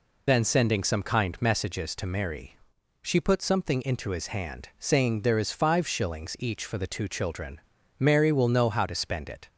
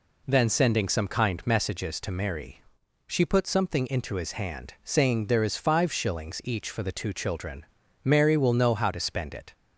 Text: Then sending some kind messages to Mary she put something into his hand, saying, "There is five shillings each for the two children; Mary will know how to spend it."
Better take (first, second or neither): second